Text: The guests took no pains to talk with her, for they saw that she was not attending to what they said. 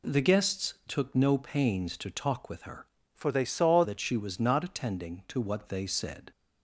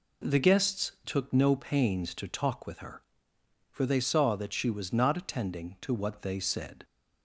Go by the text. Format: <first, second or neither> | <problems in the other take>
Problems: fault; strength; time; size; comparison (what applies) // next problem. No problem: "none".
second | changes voice from "for" to "saw"; from 3.1 to 3.8 s; 0.7 s long